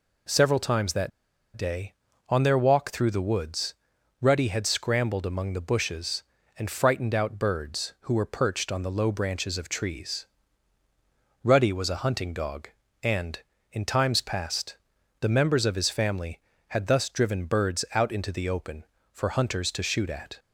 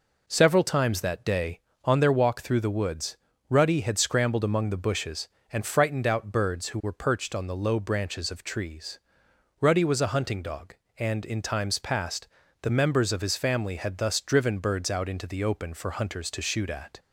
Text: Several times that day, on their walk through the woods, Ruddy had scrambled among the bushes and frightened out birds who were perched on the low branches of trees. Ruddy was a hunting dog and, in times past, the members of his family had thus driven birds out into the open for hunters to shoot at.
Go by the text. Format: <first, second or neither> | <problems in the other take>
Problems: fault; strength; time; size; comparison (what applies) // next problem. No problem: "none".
second | pauses between "that" and "day"; noticeable; at 1.1 s; 0.46 s long